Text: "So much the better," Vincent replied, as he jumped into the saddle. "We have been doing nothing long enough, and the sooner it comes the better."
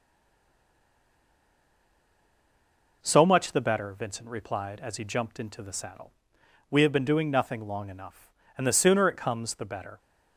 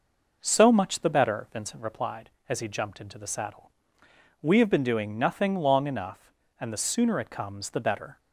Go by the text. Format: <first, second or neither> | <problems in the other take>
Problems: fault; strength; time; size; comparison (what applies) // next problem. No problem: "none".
second | stays silent before the first word; strong; until 3.0 s; 3.0 s long